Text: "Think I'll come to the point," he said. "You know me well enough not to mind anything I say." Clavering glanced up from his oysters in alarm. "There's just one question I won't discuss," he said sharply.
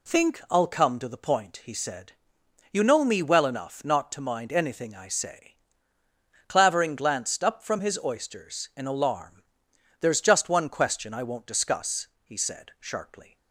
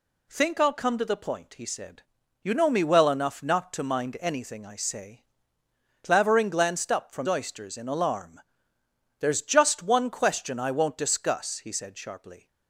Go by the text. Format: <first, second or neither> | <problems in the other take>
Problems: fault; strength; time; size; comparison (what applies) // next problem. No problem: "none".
first | skips "his"; at 7.2 s